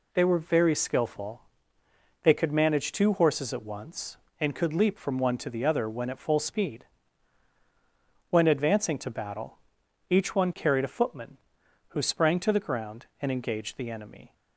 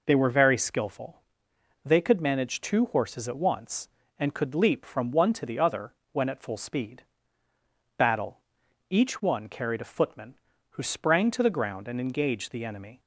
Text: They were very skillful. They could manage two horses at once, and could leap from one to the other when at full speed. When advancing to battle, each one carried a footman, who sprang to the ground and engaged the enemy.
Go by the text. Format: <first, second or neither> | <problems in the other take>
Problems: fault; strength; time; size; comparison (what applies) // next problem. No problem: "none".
first | pauses between "other" and "when"; slight; at 5.9 s; 0.16 s long // skips "When advancing to"; at 7.5 s